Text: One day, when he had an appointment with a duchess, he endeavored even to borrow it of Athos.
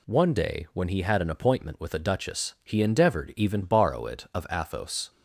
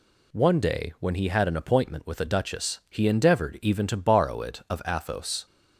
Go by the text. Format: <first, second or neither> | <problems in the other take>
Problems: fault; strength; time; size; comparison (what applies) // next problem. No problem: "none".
second | skips "to"; at 3.6 s